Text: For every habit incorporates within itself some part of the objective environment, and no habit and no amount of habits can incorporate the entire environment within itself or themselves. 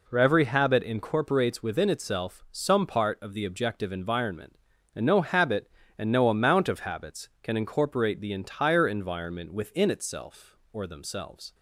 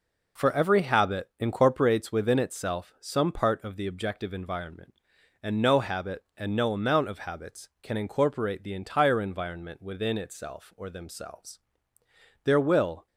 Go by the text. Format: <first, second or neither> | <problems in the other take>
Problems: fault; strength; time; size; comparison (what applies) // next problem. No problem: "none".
first | goes on to say "There will"; noticeable; from 12.4 s on; 0.62 s long